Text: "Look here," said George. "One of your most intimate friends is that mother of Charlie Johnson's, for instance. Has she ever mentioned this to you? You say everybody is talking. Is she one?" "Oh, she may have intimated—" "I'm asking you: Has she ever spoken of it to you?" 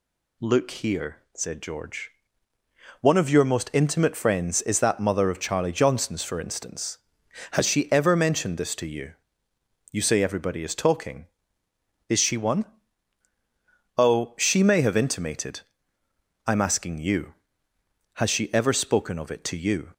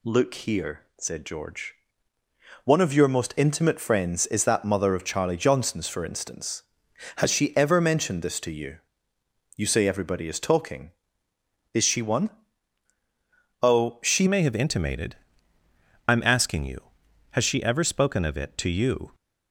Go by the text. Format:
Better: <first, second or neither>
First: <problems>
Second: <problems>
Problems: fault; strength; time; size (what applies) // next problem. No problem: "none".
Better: first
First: none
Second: changes voice at "may"; from 14.2 s on; 4.9 s long